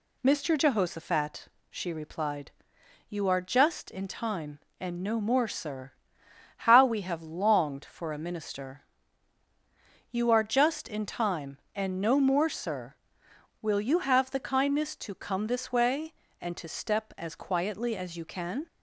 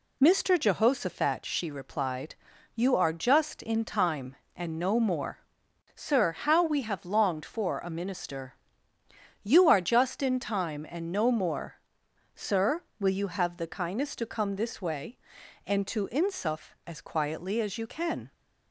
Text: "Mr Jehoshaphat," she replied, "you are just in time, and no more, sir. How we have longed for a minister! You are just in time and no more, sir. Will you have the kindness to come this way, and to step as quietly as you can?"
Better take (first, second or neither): first